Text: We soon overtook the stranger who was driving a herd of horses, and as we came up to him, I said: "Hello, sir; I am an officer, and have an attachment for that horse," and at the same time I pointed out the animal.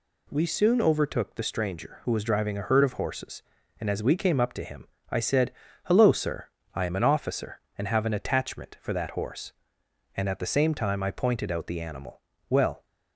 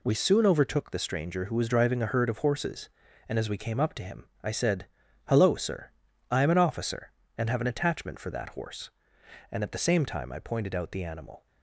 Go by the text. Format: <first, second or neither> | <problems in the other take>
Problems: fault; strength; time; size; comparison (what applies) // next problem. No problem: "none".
second | goes on to say "Well"; slight; from 12.4 s on; 0.36 s long